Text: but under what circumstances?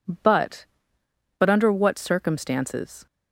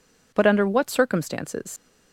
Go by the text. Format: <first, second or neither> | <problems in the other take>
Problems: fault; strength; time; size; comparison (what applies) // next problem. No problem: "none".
second | says "but" twice; at 1.3 s